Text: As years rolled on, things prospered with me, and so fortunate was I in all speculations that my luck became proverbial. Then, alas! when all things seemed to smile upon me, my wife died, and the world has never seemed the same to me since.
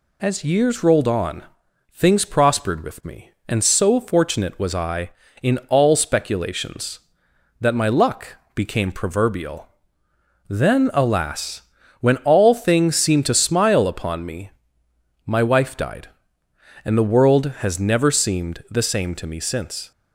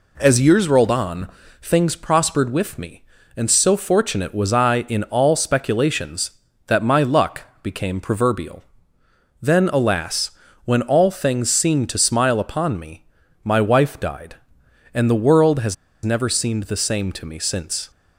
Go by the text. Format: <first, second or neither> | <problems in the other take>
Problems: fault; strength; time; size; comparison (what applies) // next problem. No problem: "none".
first | pauses between "luck" and "became"; slight; at 7.4 s; 0.20 s long; slight in the first // pauses between "has" and "never"; slight; at 15.7 s; 0.29 s long